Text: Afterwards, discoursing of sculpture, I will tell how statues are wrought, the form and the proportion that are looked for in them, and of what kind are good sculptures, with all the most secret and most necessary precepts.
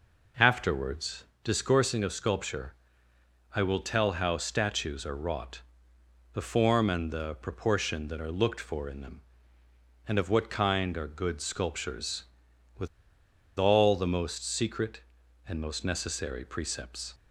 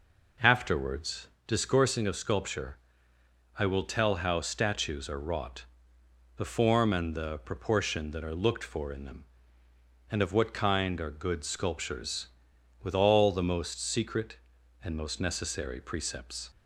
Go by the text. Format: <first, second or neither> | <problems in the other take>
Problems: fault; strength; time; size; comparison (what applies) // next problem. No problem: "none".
second | pauses between "with" and "all"; noticeable; at 12.8 s; 0.70 s long